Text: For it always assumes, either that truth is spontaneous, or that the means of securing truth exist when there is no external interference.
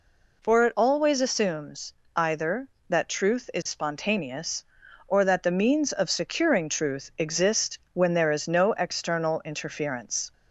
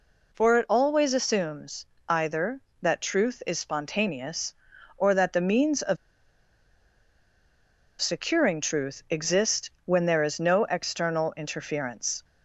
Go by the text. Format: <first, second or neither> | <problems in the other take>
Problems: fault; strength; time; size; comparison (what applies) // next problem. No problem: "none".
first | pauses between "of" and "securing"; strong; at 5.9 s; 2.0 s long // pauses between "exist" and "when"; slight; at 9.6 s; 0.16 s long; slight in the first